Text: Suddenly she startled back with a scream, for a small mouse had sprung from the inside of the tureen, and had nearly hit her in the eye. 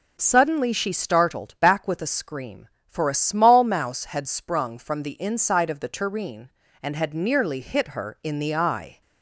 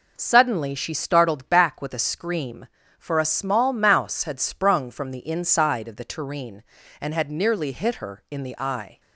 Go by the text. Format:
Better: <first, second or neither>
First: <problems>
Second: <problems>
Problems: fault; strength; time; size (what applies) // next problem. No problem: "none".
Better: neither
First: none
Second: none